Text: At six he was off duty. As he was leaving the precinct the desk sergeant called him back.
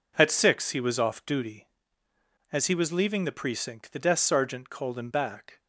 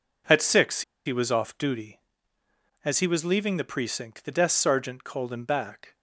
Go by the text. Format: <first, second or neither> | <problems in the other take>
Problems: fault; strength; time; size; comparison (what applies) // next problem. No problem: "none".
first | pauses between "six" and "he"; slight; at 0.8 s; 0.24 s long